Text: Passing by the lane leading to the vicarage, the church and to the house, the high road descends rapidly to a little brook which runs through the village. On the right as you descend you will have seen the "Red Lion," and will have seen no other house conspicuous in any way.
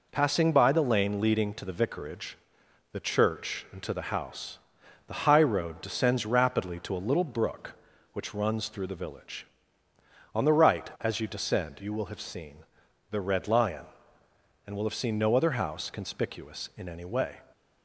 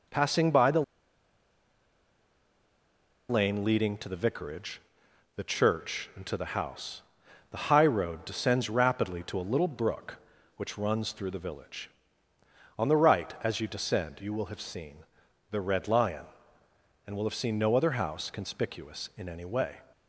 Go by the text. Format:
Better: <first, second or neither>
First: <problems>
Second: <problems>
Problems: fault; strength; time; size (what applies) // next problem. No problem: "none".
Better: first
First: pauses between "seen" and "the"; noticeable; at 12.5 s; 0.52 s long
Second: pauses between "the" and "lane"; strong; at 0.8 s; 2.4 s long // pauses between "seen" and "the"; noticeable; at 14.9 s; 0.52 s long